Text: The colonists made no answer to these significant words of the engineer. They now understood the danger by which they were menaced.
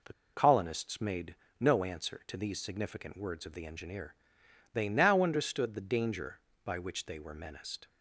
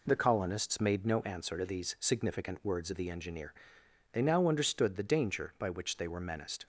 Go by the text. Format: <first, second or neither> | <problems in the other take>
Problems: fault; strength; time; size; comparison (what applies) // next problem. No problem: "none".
second | pauses between "The" and "colonists"; slight; at 0.1 s; 0.21 s long // pauses between "made" and "no"; slight; at 1.3 s; 0.24 s long